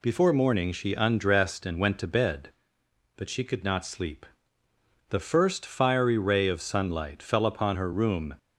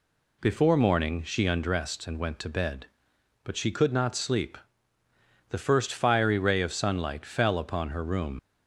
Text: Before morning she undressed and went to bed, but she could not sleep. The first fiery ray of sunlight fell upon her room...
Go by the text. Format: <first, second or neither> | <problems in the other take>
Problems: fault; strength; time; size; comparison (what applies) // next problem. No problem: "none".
first | leaves "room" unfinished; at 8.3 s; 90 ms